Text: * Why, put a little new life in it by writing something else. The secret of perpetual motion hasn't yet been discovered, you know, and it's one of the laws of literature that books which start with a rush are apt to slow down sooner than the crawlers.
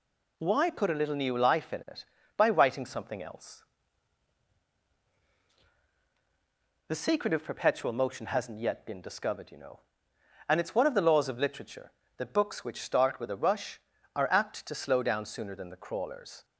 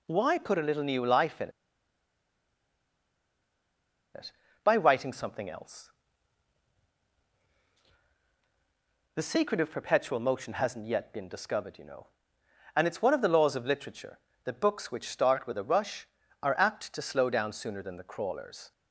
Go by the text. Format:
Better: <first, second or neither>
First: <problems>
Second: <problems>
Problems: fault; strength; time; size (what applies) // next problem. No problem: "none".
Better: first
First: none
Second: pauses between "in" and "it"; strong; at 1.4 s; 2.6 s long